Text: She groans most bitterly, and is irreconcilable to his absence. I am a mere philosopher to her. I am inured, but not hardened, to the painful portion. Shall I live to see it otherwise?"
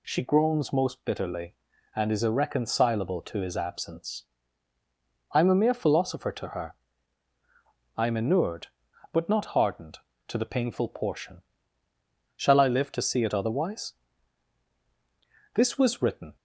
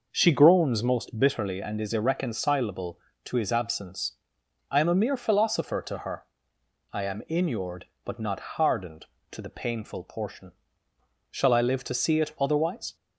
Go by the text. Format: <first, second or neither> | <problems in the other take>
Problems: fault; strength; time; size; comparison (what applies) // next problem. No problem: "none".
second | goes on to say "This was written"; noticeable; from 15.5 s on; 0.82 s long